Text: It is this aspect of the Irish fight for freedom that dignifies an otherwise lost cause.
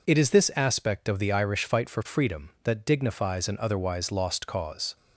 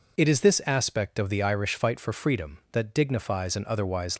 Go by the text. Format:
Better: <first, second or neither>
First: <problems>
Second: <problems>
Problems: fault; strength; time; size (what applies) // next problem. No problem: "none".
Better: first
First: none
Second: stops before "lost cause"; at 4.1 s